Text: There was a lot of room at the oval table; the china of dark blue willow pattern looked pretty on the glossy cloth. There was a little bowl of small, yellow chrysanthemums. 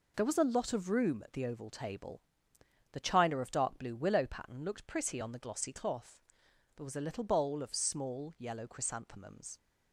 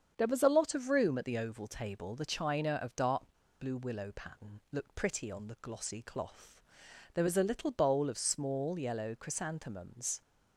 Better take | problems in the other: first | starts louder than the rest; strong; until 1.1 s; 7.5 dB // pauses between "dark" and "blue"; at 3.2 s; 0.38 s long

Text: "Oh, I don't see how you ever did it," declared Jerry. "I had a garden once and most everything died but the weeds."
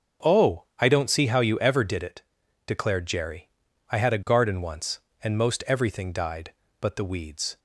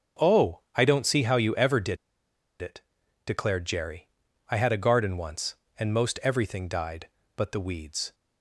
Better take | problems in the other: first | starts louder than the rest; until 1.3 s; 6 dB; noticeable in the first // pauses between "did" and "it"; noticeable; at 1.9 s; 0.65 s long

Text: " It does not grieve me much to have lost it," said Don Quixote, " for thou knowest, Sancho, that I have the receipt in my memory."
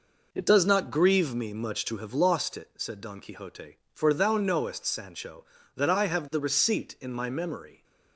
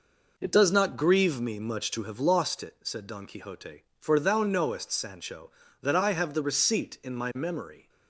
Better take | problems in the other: neither | none

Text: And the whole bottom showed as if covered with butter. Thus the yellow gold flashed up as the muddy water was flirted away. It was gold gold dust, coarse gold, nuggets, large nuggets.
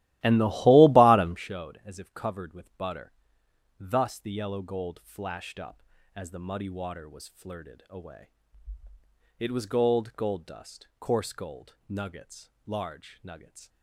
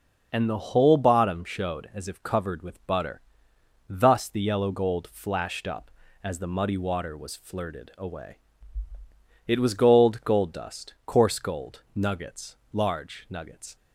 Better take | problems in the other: second | starts louder than the rest; strong; until 1.5 s; 15 dB

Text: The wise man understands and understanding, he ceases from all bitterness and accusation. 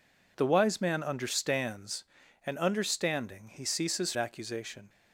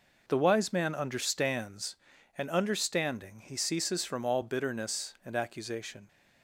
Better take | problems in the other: second | skips "from all bitterness and"; at 4.1 s

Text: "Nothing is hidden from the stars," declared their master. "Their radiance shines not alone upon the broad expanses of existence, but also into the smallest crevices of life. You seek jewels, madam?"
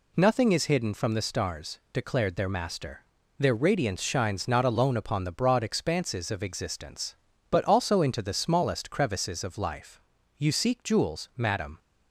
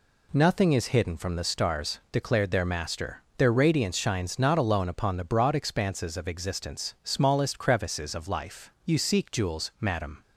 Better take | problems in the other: first | skips "but also into the"; at 6.9 s

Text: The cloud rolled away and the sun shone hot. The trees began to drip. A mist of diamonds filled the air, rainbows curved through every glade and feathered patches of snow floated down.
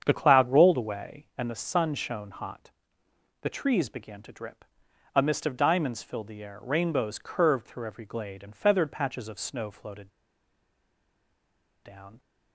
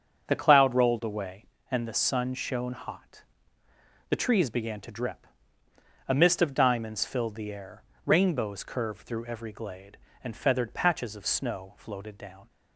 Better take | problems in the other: second | starts louder than the rest; strong; until 1.0 s; 8 dB; also in the second // pauses between "floated" and "down"; strong; at 10.0 s; 1.7 s long

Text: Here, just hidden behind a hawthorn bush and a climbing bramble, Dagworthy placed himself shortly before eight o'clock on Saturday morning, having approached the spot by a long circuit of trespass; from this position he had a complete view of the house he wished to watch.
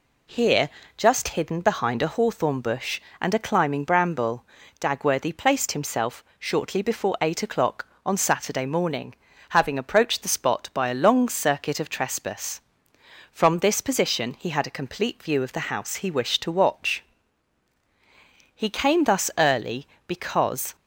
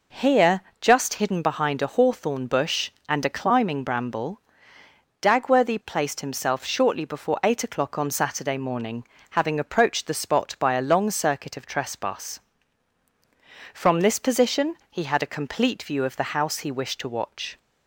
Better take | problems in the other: second | pauses between "himself" and "shortly"; slight; at 6.2 s; 0.16 s long // goes on to say "He came thus early because"; strong; from 18.5 s on; 2.2 s long

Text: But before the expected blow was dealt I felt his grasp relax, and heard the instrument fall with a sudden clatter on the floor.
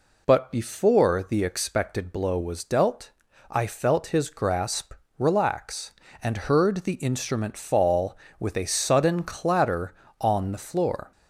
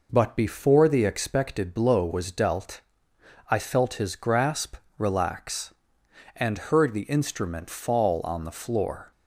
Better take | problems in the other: first | pauses between "dealt" and "I"; noticeable; at 2.8 s; 0.68 s long; also in the first // pauses between "grasp" and "relax"; slight; at 4.7 s; 0.20 s long; slight in the first // skips "with a sudden clatter"; at 8.2 s

